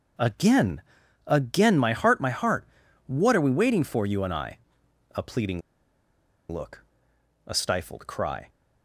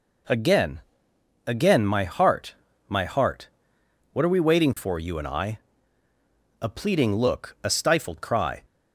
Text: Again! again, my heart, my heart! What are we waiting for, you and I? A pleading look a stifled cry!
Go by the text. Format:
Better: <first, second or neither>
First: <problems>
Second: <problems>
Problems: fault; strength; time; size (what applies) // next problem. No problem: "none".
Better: second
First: pauses between "pleading" and "look"; noticeable; at 5.6 s; 0.90 s long // pauses between "look" and "a"; noticeable; at 6.8 s; 0.66 s long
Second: none